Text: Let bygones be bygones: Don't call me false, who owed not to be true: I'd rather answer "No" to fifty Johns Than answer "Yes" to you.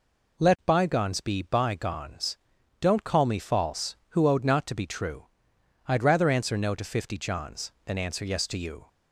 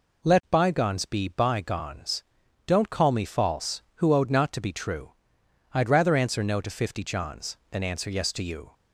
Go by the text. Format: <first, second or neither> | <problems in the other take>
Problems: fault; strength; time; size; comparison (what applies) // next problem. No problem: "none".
neither | none